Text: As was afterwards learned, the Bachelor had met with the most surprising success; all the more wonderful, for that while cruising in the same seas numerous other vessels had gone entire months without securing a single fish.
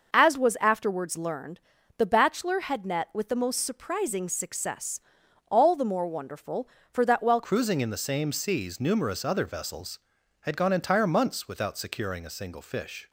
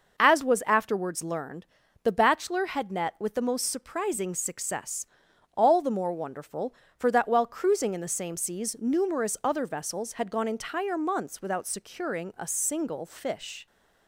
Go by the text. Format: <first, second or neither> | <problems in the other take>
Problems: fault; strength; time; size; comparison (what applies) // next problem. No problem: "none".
second | changes voice at "cruising"; from 7.4 s on; 5.6 s long